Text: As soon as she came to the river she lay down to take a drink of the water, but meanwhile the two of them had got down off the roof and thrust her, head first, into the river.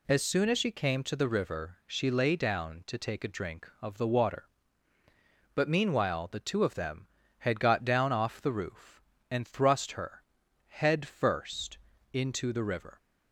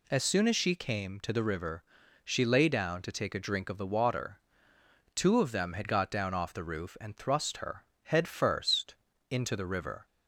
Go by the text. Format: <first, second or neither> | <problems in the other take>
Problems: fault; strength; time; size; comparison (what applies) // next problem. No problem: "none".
first | pauses between "river" and "she"; at 1.8 s; 0.42 s long // skips "but meanwhile the"; at 4.7 s